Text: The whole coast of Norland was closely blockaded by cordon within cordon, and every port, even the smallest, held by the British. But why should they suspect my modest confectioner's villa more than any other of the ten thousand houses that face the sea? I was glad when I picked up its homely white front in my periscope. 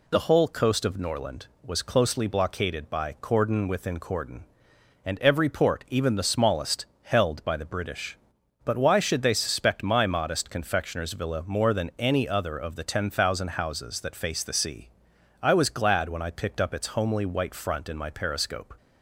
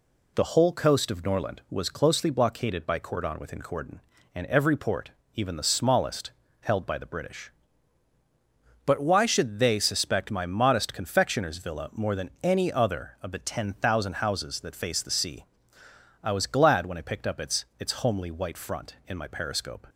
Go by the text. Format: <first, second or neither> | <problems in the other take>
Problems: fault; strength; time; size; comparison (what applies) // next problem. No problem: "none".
first | says "its" twice; at 17.7 s